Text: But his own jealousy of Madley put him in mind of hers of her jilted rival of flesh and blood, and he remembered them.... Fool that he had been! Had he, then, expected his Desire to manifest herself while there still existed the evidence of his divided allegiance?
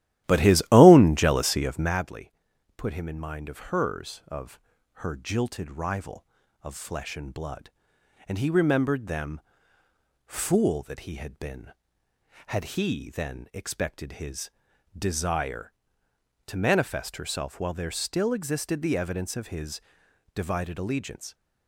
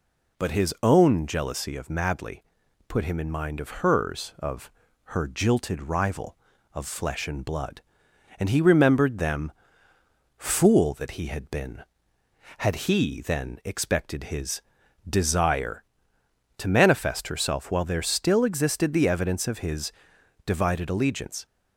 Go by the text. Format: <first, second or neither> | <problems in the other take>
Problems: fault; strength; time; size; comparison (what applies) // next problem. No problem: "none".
second | starts louder than the rest; strong; until 2.1 s; 13.5 dB // pauses between "Madley" and "put"; at 2.3 s; 0.44 s long; also in the second // pauses between "of" and "her"; at 4.5 s; 0.40 s long; also in the second // pauses between "his" and "Desire"; noticeable; at 14.4 s; 0.48 s long; noticeable in the second // pauses between "his" and "divided"; noticeable; at 19.8 s; 0.52 s long; noticeable in the second